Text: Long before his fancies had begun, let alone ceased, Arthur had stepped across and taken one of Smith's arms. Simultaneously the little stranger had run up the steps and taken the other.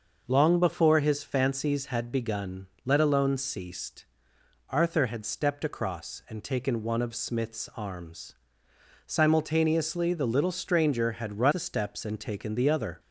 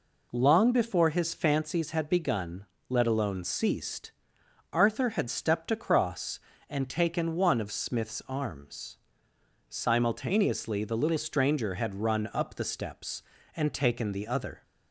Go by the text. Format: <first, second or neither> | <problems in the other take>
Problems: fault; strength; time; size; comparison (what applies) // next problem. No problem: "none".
second | skips "up"; at 11.5 s